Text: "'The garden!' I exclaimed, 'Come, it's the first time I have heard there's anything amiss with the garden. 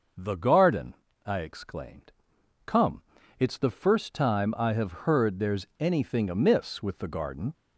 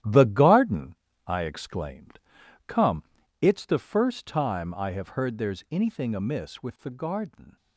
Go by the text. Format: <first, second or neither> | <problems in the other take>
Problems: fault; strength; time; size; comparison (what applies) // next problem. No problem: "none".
first | gets quieter; strong; throughout; 9 dB